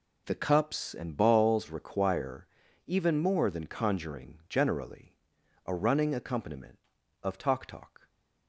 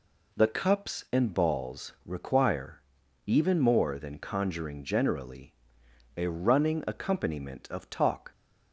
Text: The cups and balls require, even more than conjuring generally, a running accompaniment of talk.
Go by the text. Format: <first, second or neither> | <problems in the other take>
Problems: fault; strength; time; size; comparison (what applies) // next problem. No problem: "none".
second | says "talk" twice; at 7.6 s